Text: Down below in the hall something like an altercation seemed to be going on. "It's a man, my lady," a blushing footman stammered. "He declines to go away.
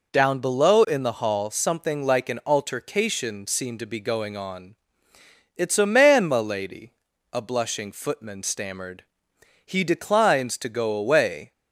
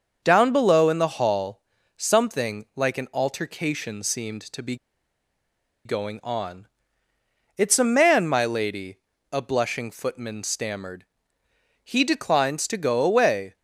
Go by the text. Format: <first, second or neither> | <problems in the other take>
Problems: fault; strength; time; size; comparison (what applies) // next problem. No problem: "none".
first | starts louder than the rest; until 1.2 s; 6.5 dB // pauses between "hall" and "something"; slight; at 1.5 s; 0.36 s long // pauses between "be" and "going"; at 4.7 s; 1.0 s long